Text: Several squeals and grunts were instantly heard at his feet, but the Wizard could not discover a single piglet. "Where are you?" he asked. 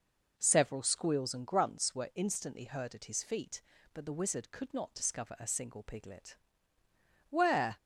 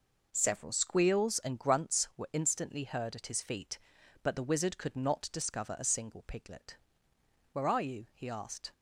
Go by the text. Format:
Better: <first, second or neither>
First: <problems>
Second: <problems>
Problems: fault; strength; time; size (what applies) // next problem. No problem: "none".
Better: second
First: stops before "are you he asked"; at 7.7 s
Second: none